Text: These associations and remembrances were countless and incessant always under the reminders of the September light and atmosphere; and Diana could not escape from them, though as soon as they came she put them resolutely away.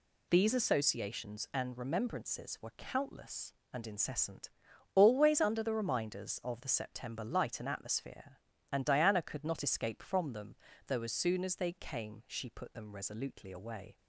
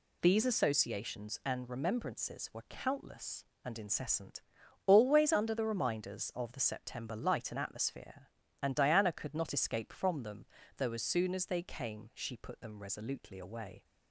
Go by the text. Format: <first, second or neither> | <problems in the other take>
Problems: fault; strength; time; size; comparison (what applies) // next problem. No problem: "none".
neither | pauses between "incessant" and "always"; the same in both